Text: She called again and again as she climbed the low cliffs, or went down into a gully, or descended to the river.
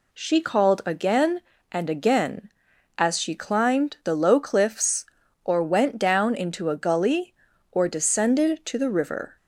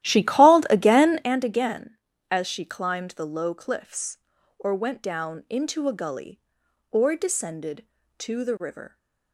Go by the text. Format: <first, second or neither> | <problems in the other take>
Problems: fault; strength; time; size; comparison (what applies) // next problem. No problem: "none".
first | starts louder than the rest; strong; until 1.3 s; 13.5 dB